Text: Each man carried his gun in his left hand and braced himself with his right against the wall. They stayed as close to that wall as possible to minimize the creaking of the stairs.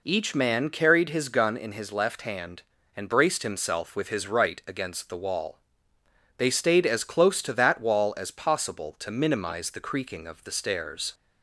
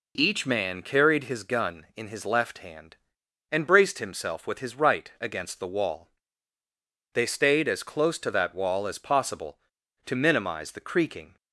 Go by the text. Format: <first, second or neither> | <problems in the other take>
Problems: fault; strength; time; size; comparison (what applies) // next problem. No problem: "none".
first | stops before "of the stairs"; at 11.3 s